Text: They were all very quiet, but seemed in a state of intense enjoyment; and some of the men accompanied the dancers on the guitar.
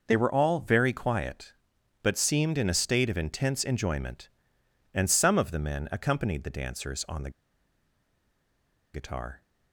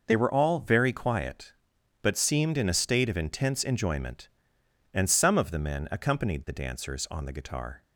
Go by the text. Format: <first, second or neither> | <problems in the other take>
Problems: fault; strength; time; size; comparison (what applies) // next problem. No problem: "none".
second | pauses between "the" and "guitar"; strong; at 7.2 s; 1.6 s long